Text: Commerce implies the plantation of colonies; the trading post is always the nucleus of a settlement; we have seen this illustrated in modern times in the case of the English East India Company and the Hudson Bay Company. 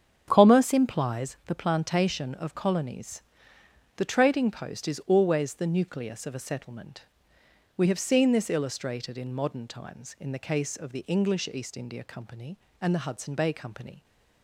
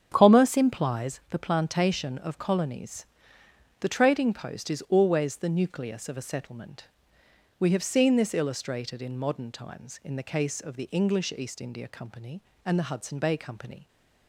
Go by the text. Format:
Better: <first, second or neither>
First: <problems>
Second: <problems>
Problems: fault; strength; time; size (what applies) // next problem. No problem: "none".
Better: neither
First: starts louder than the rest; strong; until 1.2 s; 7.5 dB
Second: starts louder than the rest; strong; until 1.1 s; 7.5 dB